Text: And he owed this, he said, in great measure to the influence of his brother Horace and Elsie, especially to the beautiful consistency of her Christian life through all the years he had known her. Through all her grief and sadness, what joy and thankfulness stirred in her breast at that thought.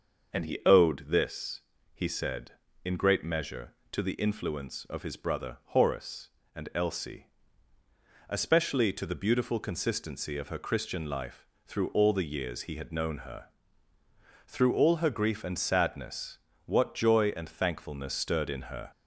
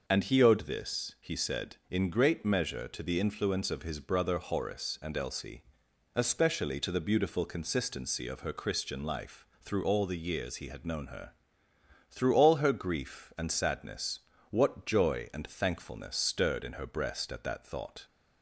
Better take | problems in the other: second | starts louder than the rest; until 1.4 s; 6.5 dB // pauses between "life" and "through"; slight; at 11.4 s; 0.22 s long; slight in the second // stops before "breast at that thought"; at 18.9 s

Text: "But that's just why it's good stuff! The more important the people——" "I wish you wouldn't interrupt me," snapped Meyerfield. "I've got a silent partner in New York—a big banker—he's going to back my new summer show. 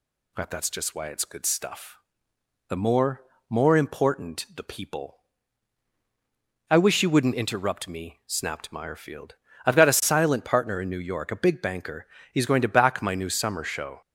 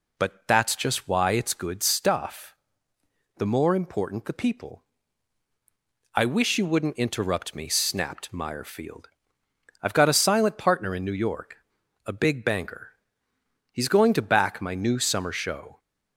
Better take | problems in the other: second | says "more" twice; at 3.5 s

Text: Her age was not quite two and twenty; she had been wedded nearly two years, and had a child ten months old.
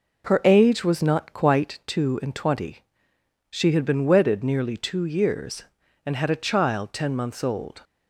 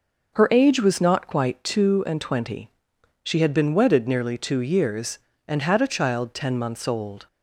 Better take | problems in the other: neither | none

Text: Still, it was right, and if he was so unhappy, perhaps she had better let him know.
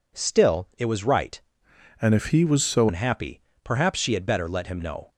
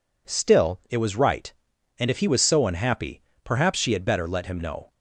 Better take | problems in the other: second | changes voice from "and" to "so"; from 2.0 to 2.8 s; 0.8 s long

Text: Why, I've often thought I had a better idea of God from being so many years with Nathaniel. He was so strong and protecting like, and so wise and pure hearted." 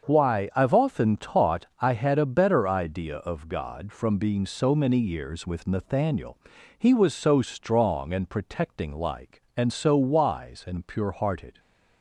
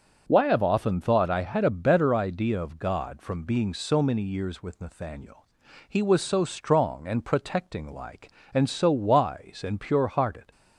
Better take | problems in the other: second | starts louder than the rest; until 1.0 s; 6.5 dB; also in the second // says "taught" for "thought"; at 1.1 s

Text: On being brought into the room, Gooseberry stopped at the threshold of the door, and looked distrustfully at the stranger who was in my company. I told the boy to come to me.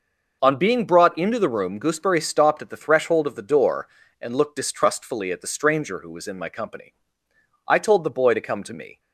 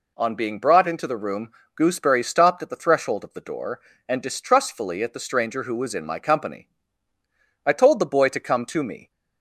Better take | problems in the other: first | skips "looked"; at 4.2 s

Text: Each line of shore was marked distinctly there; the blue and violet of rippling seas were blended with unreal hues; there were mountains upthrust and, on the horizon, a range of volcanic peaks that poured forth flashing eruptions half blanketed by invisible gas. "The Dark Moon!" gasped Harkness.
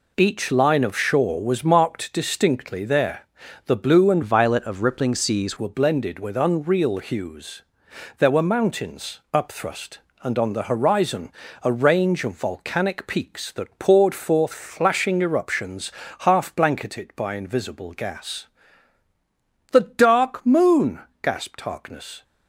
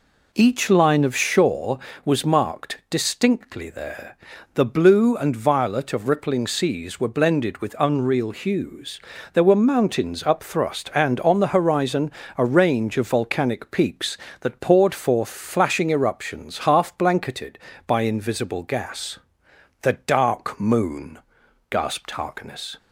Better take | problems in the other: second | changes voice from "violet" to "seas"; from 4.2 to 5.5 s; 1.3 s long // pauses between "eruptions" and "half"; slight; at 15.9 s; 0.30 s long

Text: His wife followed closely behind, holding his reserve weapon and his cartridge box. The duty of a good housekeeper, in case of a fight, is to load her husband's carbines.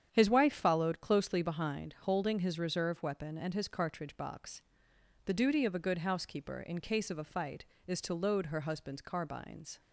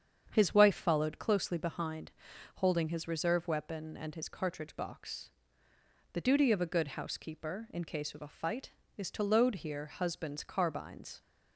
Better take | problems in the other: first | starts louder than the rest; strong; until 1.3 s; 8 dB; strong in the first // says "here" for "her"; at 9.5 s

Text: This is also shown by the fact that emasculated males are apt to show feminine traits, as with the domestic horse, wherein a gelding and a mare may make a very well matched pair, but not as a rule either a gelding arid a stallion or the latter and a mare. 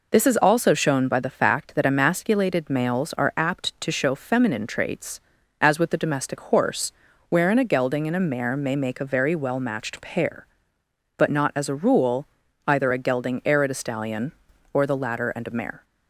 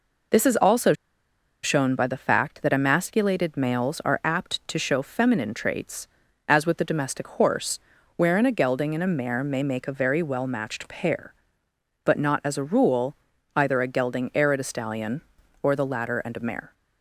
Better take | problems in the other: first | pauses between "also" and "shown"; noticeable; at 0.9 s; 0.70 s long // pauses between "rule" and "either"; at 13.1 s; 0.40 s long; also in the first

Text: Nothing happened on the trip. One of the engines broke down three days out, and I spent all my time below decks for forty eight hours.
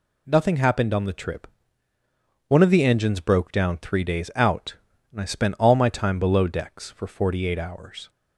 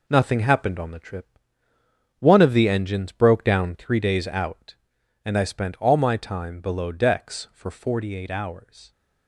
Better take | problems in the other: first | gets quieter; strong; throughout; 8 dB

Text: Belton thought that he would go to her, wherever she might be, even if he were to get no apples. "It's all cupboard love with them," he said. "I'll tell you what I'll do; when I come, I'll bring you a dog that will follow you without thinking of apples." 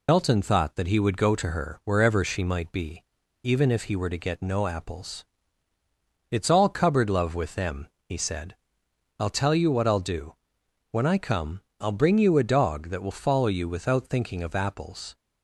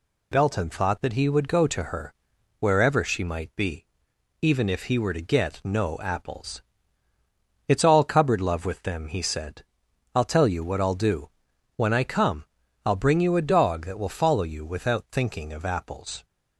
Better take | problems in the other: second | loses the start of "Belton"; at 0.0 s; 65 ms

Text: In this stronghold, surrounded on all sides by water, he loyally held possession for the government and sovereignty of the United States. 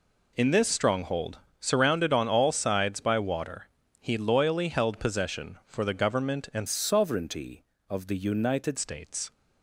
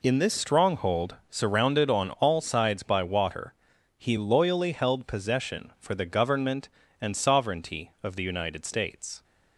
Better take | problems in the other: second | changes voice from "sovereignty" to "United"; from 6.6 to 8.7 s; 2.1 s long

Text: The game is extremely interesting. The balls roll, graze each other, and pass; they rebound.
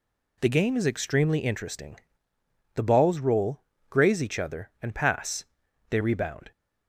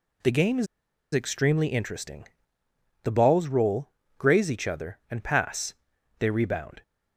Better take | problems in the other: first | pauses between "is" and "extremely"; noticeable; at 0.6 s; 0.47 s long

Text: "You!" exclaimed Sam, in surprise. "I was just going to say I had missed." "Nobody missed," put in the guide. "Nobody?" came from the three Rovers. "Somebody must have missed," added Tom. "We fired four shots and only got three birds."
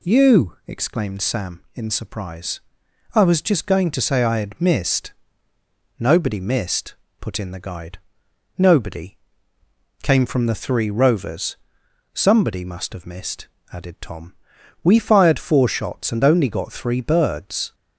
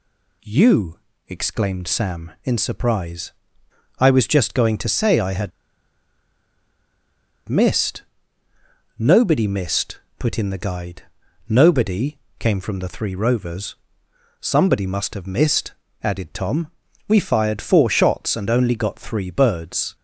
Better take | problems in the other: first | pauses between "had" and "missed"; strong; at 5.5 s; 1.9 s long

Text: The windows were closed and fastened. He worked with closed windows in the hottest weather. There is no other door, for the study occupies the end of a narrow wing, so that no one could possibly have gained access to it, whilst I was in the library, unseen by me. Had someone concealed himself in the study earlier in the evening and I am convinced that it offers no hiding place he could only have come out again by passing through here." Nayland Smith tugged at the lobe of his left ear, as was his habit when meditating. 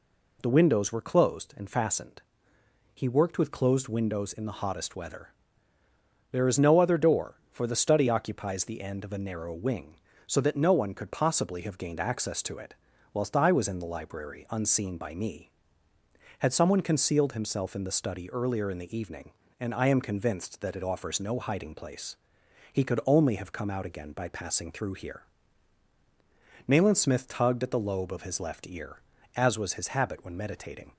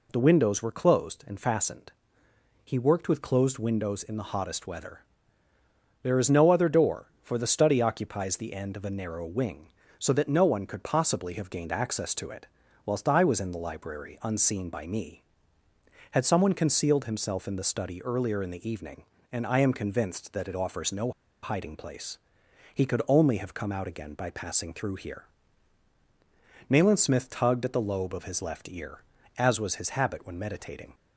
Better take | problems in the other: first | pauses between "no" and "hiding"; slight; at 21.1 s; 0.30 s long // pauses between "place" and "he"; noticeable; at 22.1 s; 0.58 s long; noticeable in the first

